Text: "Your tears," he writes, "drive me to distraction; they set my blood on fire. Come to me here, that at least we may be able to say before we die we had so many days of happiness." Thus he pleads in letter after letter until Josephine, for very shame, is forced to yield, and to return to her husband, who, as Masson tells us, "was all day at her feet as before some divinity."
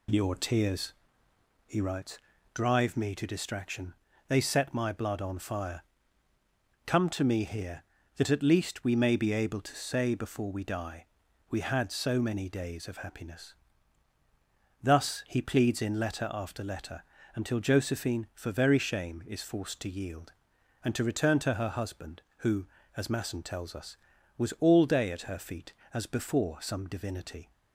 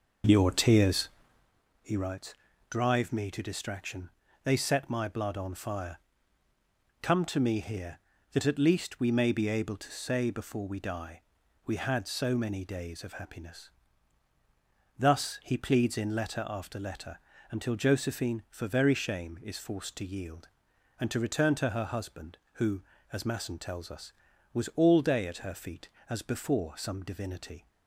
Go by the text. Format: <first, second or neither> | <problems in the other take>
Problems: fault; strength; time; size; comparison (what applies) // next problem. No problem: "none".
first | starts louder than the rest; noticeable; until 1.5 s; 6 dB // pauses between "die" and "we"; noticeable; at 11.2 s; 0.46 s long; noticeable in the first // pauses between "letter" and "until"; slight; at 17.1 s; 0.32 s long; slight in the first